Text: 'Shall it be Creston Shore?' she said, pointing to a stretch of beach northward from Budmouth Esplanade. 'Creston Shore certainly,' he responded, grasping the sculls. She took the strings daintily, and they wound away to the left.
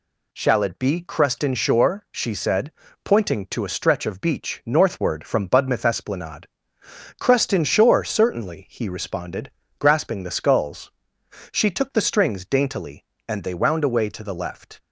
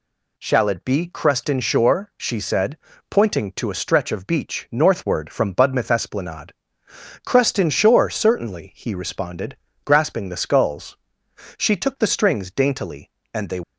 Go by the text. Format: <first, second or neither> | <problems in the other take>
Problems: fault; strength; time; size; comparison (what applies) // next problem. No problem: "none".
first | stops before "wound away to the left"; at 13.6 s